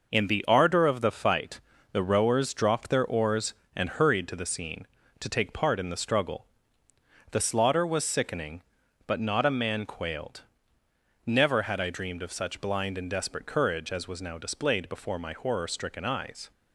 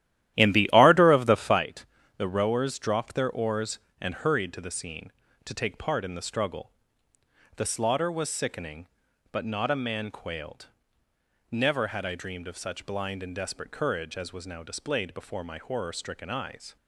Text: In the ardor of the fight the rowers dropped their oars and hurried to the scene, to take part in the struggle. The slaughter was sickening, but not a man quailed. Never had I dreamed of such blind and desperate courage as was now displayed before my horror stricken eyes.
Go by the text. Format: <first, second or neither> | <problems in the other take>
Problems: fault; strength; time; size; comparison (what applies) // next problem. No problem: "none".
first | starts louder than the rest; strong; until 1.6 s; 13 dB // pauses between "fight" and "the"; slight; at 1.8 s; 0.30 s long; slight in the first